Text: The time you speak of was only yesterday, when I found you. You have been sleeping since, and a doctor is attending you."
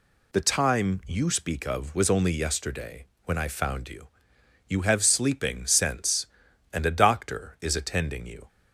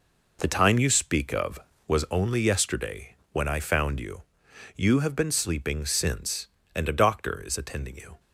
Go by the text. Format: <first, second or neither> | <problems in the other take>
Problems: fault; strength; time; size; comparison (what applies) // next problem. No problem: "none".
second | skips "been"; at 5.0 s